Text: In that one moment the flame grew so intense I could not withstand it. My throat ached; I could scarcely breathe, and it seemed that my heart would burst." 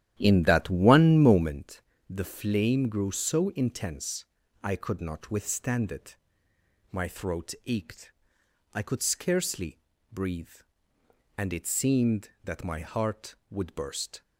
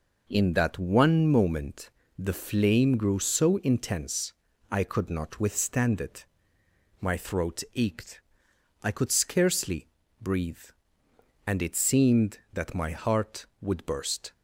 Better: second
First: starts louder than the rest; strong; until 1.6 s; 11.5 dB // pauses between "moment" and "the"; slight; at 1.8 s; 0.26 s long // pauses between "intense" and "I"; at 4.2 s; 0.38 s long // pauses between "scarcely" and "breathe"; slight; at 9.8 s; 0.32 s long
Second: pauses between "moment" and "the"; slight; at 1.9 s; 0.26 s long // pauses between "intense" and "I"; at 4.3 s; 0.38 s long // pauses between "scarcely" and "breathe"; slight; at 9.9 s; 0.32 s long

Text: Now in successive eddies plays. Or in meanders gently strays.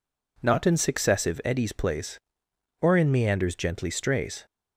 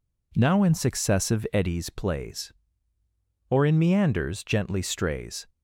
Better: second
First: says "Not" for "Now"; at 0.4 s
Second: none

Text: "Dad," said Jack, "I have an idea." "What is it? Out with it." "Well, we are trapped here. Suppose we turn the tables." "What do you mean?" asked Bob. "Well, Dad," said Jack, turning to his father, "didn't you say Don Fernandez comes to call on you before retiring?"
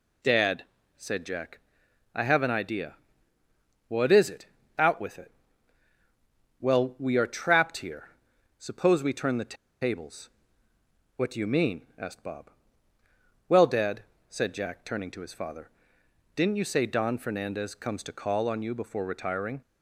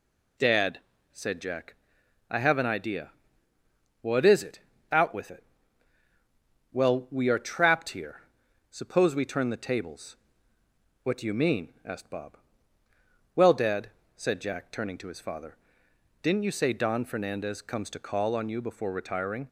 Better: second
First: pauses between "the" and "tables"; slight; at 9.5 s; 0.25 s long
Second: none

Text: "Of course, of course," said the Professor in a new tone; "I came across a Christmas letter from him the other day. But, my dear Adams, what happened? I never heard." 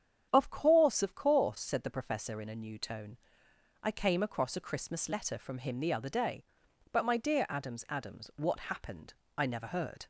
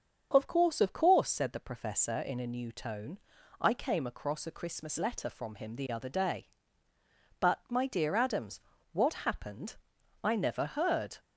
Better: second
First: starts louder than the rest; strong; until 1.3 s; 8.5 dB // says "Adams" twice; at 7.8 s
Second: starts louder than the rest; until 1.3 s; 6.5 dB

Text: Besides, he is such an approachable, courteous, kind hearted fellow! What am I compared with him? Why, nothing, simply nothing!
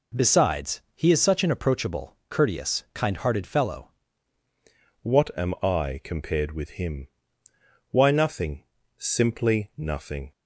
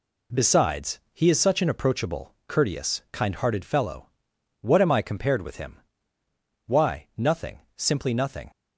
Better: second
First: changes voice at "What"; from 5.0 s on; 5.3 s long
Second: none

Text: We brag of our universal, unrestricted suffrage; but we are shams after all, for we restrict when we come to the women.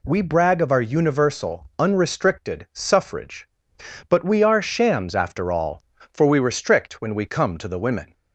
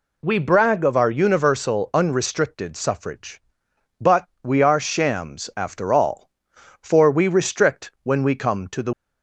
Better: first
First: none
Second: pauses between "but" and "we"; slight; at 4.2 s; 0.16 s long // stops before "women"; at 8.9 s

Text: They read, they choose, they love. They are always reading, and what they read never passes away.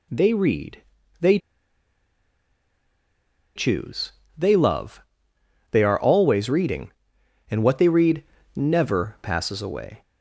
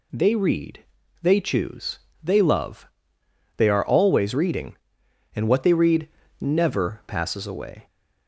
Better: second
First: pauses between "they" and "choose"; strong; at 1.3 s; 2.1 s long // pauses between "read" and "never"; slight; at 8.2 s; 0.32 s long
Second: pauses between "read" and "never"; slight; at 6.0 s; 0.32 s long

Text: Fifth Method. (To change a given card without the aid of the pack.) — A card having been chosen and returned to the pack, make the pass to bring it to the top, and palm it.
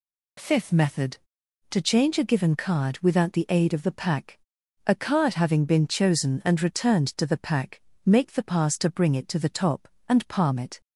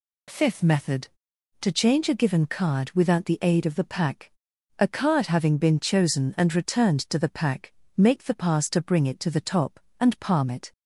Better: neither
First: none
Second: none

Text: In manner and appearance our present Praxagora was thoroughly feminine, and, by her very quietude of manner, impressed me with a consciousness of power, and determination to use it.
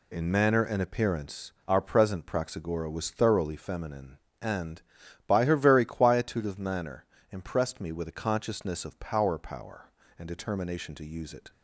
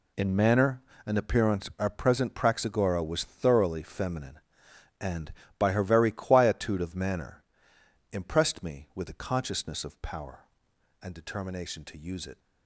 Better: second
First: says "power" twice; at 9.3 s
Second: none

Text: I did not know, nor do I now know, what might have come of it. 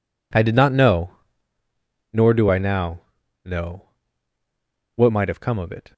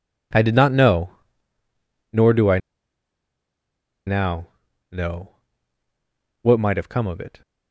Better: first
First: pauses between "now" and "know"; at 3.0 s; 0.42 s long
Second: pauses between "I" and "now"; strong; at 2.5 s; 1.4 s long // pauses between "now" and "know"; at 4.4 s; 0.42 s long

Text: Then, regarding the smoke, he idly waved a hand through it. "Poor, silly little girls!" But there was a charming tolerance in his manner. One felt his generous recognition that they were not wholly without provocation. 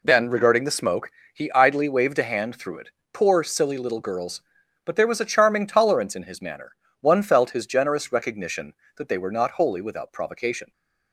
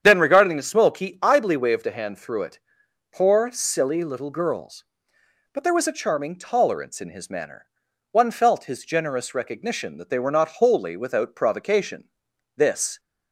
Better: first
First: none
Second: starts louder than the rest; strong; until 1.0 s; 8.5 dB // goes on to say "This"; slight; from 12.5 s on; 0.44 s long

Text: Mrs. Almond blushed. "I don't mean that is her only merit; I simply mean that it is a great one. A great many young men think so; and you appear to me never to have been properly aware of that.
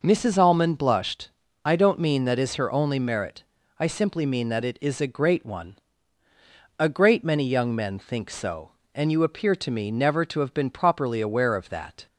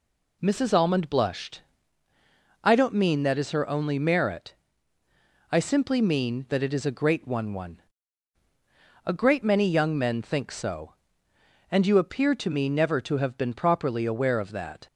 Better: first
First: none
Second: says "one" twice; at 7.5 s

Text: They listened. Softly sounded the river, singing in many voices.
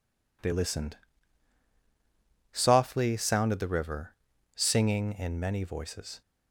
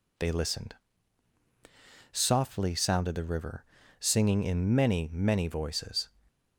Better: first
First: none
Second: says "many" twice; at 5.1 s // stays silent after the last word; slight; from 6.0 s on; 0.5 s long

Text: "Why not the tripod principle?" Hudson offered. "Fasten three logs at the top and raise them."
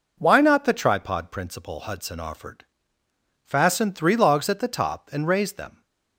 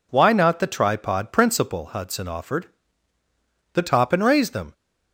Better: first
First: none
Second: skips "Fasten three logs at"; at 3.2 s

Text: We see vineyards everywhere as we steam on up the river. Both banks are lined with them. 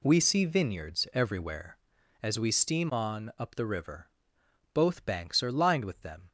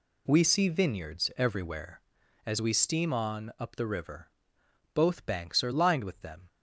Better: neither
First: none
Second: none

